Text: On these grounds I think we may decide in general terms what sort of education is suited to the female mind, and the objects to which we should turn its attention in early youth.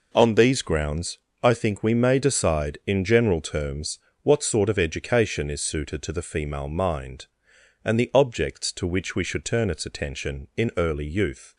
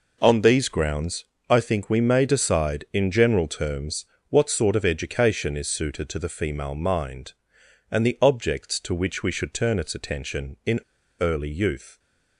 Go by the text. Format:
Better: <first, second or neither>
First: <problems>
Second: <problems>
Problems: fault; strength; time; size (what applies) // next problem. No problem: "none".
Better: first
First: pauses between "grounds" and "I"; slight; at 1.1 s; 0.22 s long // pauses between "terms" and "what"; slight; at 3.9 s; 0.26 s long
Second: pauses between "grounds" and "I"; slight; at 1.2 s; 0.22 s long // pauses between "terms" and "what"; slight; at 4.0 s; 0.26 s long // pauses between "in" and "early"; at 10.8 s; 0.38 s long